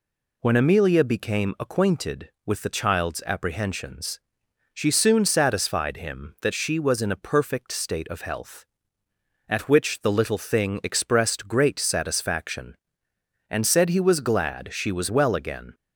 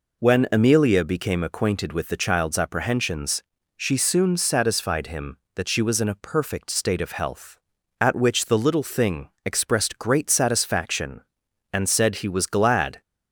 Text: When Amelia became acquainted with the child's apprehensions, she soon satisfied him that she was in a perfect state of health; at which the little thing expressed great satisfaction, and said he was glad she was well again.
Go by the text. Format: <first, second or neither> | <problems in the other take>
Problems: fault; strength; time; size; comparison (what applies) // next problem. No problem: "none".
first | pauses between "thing" and "expressed"; slight; at 9.2 s; 0.16 s long // stops before "she was well again"; at 13.0 s